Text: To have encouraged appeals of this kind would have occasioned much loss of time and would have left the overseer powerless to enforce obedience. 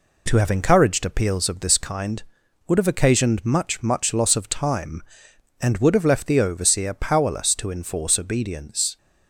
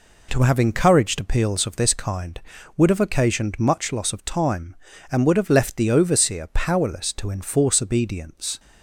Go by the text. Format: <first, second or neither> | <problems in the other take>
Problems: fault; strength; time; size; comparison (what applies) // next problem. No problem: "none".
second | says "much" twice; at 3.8 s